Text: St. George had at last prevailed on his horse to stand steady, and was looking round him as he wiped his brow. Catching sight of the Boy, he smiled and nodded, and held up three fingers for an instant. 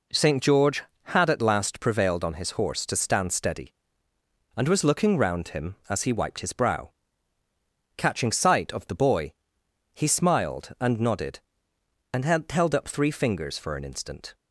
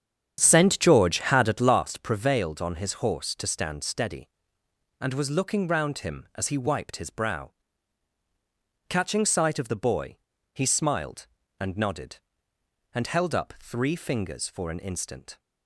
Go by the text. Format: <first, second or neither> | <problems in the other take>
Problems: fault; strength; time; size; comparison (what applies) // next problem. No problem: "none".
first | starts louder than the rest; strong; until 1.9 s; 8.5 dB